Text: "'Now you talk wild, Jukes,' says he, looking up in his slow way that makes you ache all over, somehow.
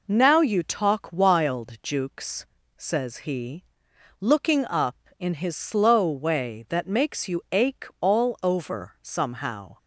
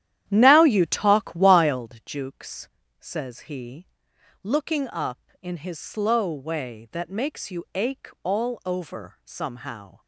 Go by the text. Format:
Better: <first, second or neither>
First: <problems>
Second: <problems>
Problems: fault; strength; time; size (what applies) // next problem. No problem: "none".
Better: first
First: pauses between "ache" and "all"; slight; at 7.8 s; 0.16 s long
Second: starts louder than the rest; strong; until 1.9 s; 11 dB // pauses between "ache" and "all"; slight; at 8.0 s; 0.16 s long